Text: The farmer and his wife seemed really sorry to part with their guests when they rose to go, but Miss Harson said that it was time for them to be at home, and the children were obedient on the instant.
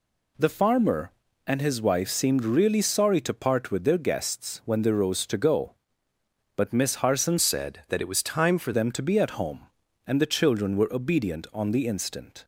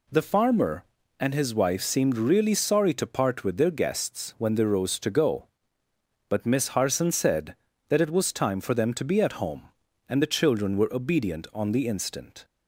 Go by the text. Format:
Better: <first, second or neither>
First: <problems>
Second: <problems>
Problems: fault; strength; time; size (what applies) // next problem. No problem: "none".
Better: second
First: changes voice from "said" to "for"; from 7.3 to 8.7 s; 1.4 s long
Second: none